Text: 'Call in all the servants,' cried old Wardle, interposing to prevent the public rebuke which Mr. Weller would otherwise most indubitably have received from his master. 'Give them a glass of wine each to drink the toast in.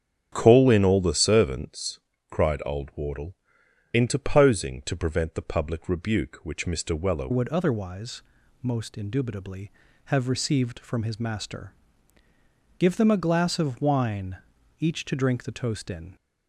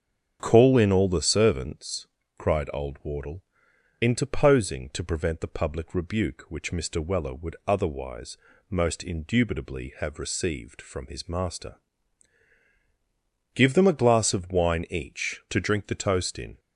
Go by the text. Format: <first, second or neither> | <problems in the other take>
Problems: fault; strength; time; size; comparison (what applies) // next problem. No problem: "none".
second | starts louder than the rest; strong; until 1.3 s; 8.5 dB; strong in the second // changes voice at "would"; from 7.3 s on; 8.8 s long // pauses between "otherwise" and "most"; at 8.2 s; 0.40 s long; slight in the second // pauses between "wine" and "each"; at 14.3 s; 0.42 s long